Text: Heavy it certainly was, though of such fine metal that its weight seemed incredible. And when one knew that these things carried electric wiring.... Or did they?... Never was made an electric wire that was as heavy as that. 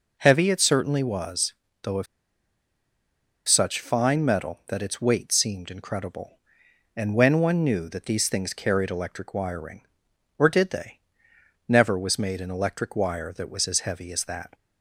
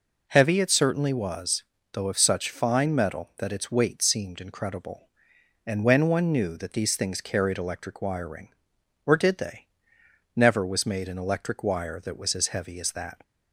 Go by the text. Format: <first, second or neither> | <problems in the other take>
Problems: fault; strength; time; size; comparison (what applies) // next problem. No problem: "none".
second | pauses between "of" and "such"; strong; at 2.0 s; 1.4 s long